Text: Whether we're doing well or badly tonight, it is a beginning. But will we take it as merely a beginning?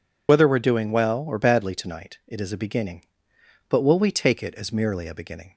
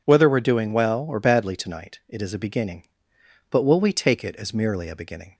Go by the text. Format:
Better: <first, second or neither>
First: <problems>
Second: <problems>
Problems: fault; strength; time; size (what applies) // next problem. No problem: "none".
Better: second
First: loses the start of "Whether"; at 0.2 s; 55 ms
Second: none